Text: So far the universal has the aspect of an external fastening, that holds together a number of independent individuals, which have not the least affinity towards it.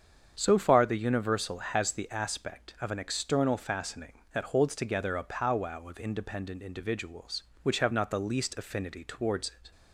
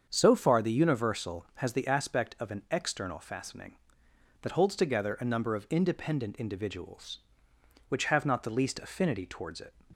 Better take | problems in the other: second | starts louder than the rest; strong; until 1.3 s; 7.5 dB; strong in the second // says "powwow" for "number"; at 5.2 s

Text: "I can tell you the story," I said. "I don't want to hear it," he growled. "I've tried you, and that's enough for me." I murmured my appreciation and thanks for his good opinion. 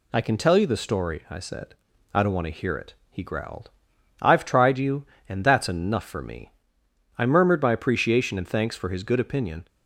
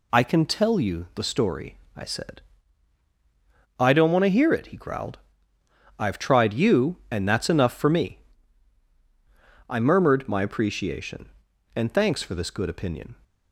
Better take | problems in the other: first | says "this" for "his"; at 12.3 s

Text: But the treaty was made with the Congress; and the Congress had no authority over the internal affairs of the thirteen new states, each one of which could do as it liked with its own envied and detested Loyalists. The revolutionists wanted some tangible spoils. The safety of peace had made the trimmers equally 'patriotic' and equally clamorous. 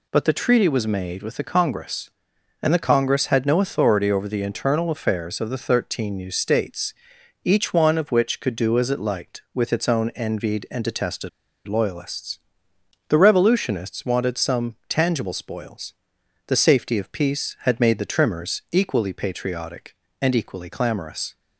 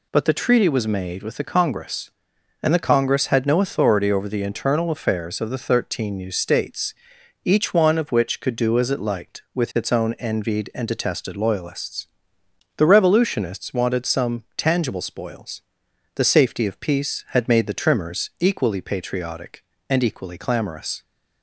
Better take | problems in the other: second | pauses between "detested" and "Loyalists"; at 11.2 s; 0.38 s long

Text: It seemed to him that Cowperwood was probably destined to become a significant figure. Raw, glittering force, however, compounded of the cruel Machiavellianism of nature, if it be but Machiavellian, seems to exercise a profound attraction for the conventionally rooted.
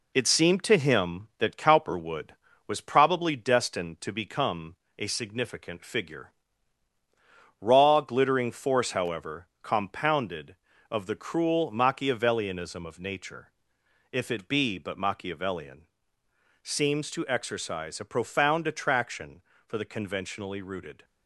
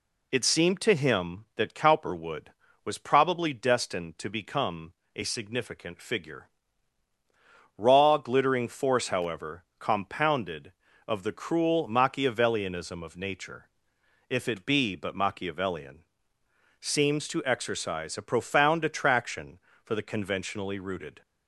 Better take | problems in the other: second | gets quieter; throughout; 3.5 dB // pauses between "become" and "a"; slight; at 4.7 s; 0.22 s long; slight in the second

